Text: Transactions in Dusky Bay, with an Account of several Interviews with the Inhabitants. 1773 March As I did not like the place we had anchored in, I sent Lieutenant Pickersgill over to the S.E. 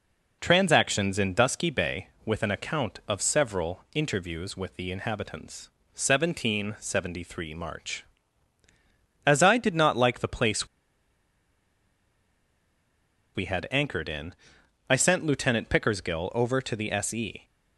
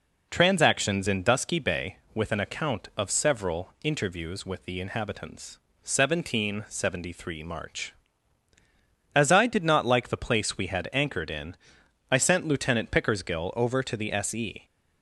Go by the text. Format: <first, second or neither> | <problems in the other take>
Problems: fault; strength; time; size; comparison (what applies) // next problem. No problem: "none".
second | pauses between "place" and "we"; strong; at 10.6 s; 2.6 s long